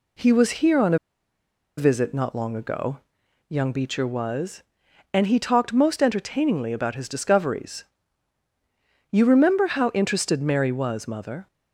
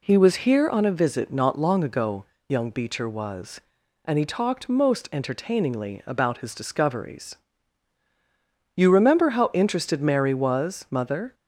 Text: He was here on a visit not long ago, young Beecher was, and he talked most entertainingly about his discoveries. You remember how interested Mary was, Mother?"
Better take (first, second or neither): second